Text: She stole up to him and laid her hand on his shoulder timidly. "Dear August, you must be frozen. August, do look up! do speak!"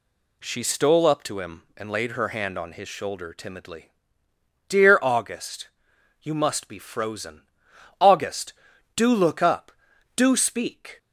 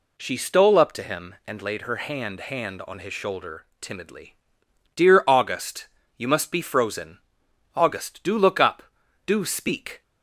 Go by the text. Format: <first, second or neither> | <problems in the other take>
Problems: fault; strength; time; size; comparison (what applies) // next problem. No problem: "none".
first | says "hand" twice; at 2.3 s